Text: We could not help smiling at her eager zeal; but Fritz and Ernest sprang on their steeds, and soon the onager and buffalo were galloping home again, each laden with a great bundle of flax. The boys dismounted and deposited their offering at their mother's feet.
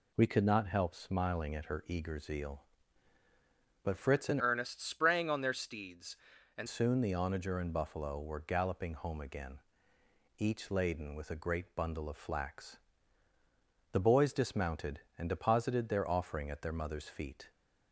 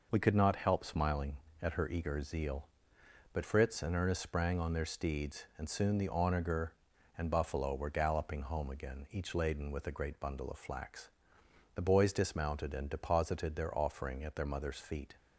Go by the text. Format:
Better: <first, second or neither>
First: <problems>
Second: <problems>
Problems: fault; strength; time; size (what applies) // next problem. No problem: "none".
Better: second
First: changes voice from "Ernest" to "and"; from 4.3 to 6.6 s; 2.3 s long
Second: none